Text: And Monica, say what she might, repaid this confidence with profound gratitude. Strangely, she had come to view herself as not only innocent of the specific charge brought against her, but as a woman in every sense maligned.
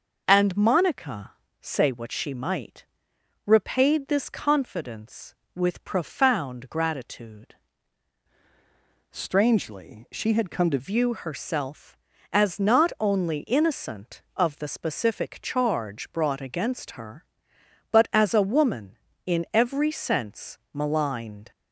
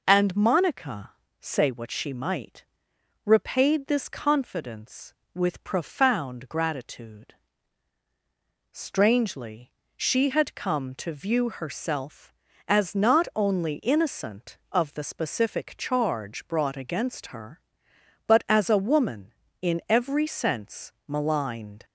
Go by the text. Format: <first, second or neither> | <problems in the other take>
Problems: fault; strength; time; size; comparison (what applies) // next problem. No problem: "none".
second | changes voice from "Strangely" to "to"; from 9.1 to 10.7 s; 1.6 s long